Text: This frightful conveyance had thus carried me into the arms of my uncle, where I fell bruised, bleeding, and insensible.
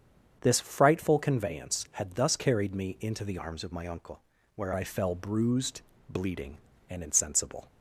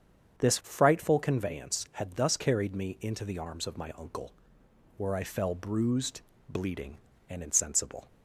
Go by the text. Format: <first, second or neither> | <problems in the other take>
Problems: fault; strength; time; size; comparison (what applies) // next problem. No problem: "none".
second | starts louder than the rest; strong; until 1.4 s; 7.5 dB; strong in the second // changes voice from "arms" to "where"; from 3.3 to 4.7 s; 1.4 s long